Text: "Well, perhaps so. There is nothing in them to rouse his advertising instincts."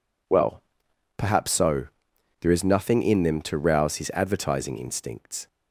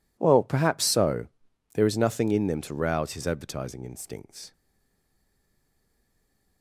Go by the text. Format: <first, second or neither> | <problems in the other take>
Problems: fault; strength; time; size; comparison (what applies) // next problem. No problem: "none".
first | stays silent after the last word; from 4.5 s on; 2.1 s long